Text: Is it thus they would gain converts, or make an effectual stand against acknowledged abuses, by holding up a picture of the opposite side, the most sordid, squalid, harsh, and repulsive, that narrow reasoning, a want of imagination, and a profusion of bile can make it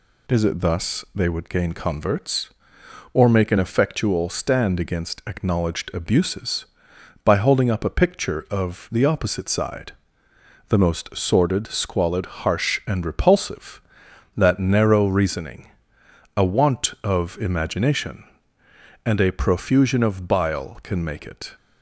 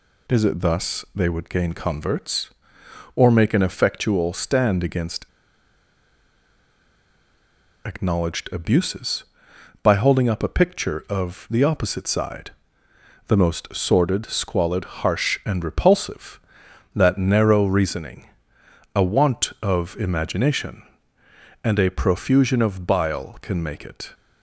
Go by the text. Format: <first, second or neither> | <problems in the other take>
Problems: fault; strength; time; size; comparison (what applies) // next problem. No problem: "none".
first | pauses between "against" and "acknowledged"; strong; at 5.2 s; 2.5 s long